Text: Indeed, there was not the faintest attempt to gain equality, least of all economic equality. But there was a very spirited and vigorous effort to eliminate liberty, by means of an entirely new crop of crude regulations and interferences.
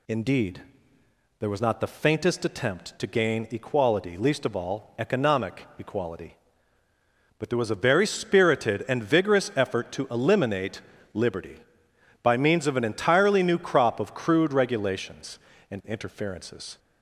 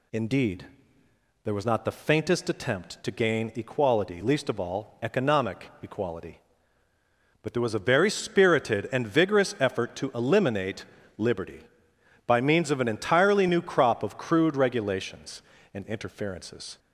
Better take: neither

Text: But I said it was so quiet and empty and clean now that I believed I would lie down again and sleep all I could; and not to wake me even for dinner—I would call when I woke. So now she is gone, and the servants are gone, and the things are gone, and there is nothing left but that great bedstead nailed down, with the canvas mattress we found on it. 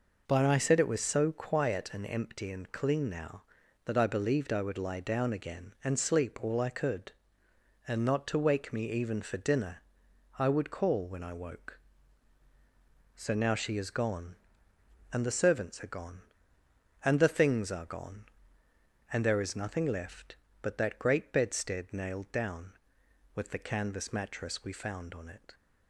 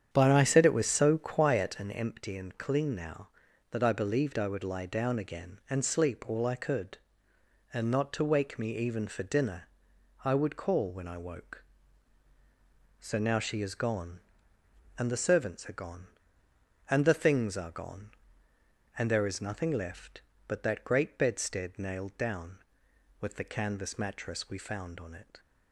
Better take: first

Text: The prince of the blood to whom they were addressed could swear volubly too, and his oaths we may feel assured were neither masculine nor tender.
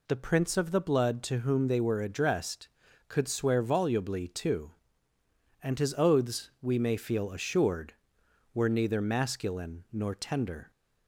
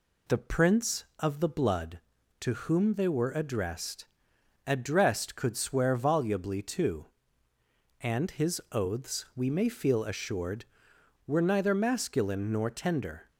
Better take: first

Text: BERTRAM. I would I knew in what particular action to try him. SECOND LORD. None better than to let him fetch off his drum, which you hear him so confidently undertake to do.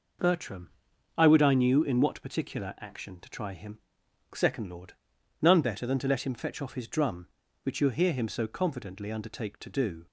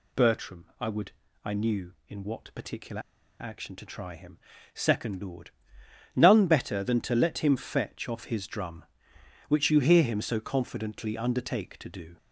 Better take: first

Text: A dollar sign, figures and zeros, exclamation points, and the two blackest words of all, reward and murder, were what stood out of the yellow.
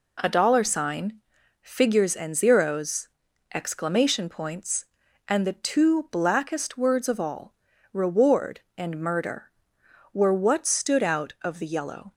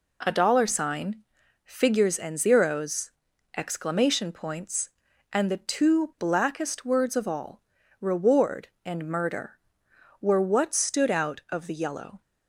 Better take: neither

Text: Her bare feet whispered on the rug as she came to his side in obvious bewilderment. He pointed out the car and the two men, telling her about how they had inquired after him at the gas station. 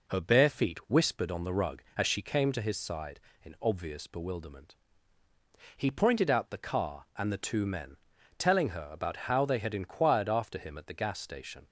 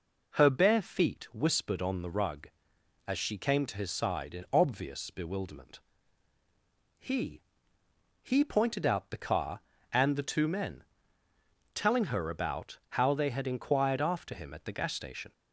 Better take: first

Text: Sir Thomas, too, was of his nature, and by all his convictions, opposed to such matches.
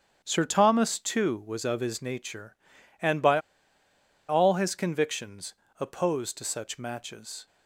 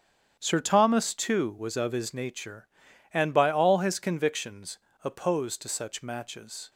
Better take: second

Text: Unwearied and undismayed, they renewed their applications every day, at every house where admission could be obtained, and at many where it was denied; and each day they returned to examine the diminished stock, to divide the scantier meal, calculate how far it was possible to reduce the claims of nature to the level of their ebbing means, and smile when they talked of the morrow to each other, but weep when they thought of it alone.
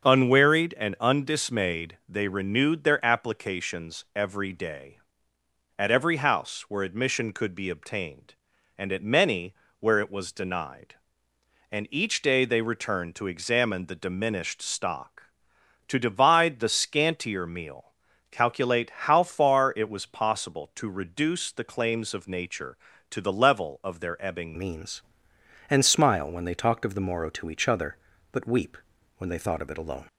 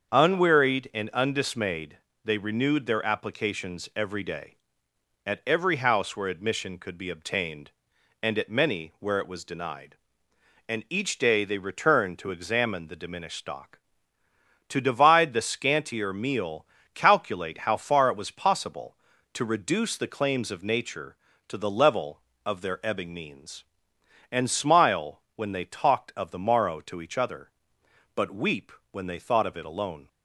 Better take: second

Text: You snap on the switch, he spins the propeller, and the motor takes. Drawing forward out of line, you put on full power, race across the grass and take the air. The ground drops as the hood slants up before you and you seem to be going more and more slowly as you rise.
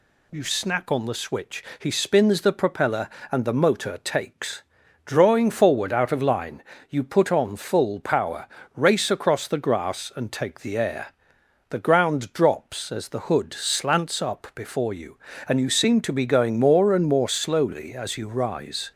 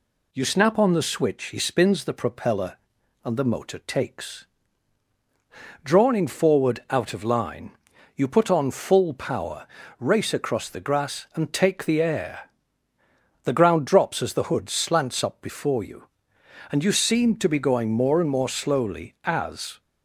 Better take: first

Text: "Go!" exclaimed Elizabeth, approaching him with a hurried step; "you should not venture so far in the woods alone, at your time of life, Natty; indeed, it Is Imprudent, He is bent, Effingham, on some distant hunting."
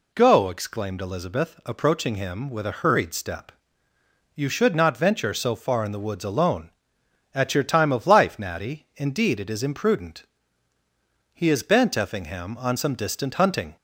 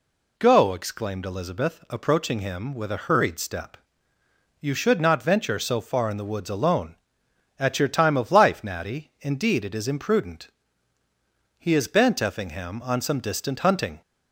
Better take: neither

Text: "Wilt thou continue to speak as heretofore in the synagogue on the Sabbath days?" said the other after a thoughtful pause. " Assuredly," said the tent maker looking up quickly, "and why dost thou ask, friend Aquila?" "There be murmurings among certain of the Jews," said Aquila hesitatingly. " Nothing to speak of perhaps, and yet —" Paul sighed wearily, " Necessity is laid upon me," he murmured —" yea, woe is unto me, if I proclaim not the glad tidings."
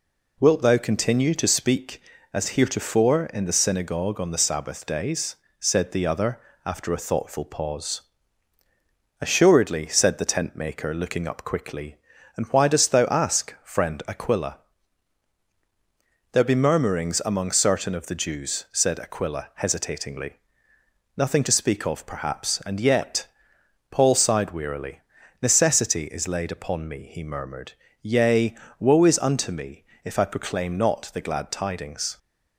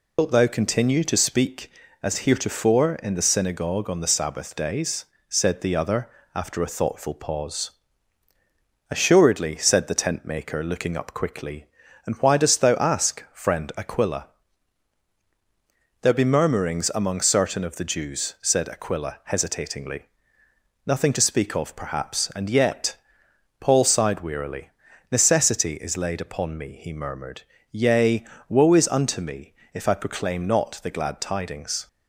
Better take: first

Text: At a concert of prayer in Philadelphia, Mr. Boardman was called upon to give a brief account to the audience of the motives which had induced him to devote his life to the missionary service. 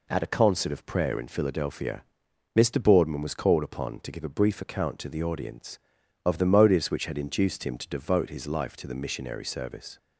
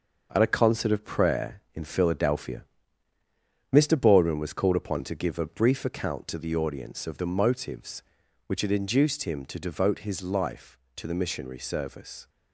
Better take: first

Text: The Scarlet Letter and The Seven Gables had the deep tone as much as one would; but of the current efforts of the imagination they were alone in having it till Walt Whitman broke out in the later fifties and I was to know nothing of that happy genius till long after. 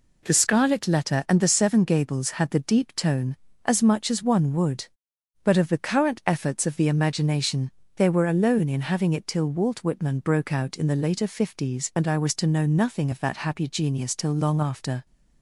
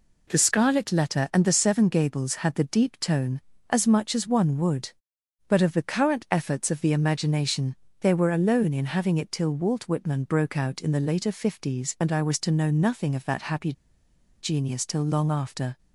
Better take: first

